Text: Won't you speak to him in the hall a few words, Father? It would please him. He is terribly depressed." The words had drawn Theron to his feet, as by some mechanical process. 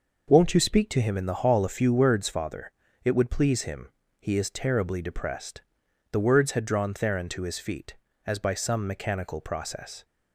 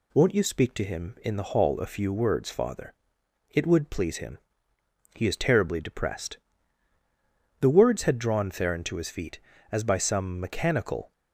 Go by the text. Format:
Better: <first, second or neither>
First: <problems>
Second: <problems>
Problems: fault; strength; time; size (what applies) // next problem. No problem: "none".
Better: first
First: none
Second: stops before "process"; at 11.1 s